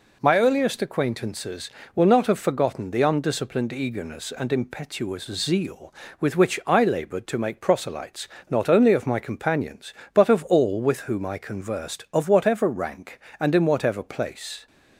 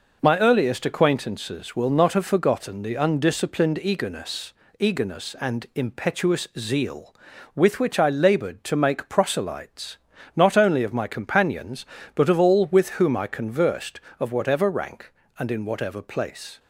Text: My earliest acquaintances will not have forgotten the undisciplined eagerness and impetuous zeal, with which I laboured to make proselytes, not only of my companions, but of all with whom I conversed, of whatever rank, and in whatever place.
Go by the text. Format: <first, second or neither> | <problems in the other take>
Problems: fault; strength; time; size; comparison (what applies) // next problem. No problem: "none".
first | says "eagerness" twice; at 4.7 s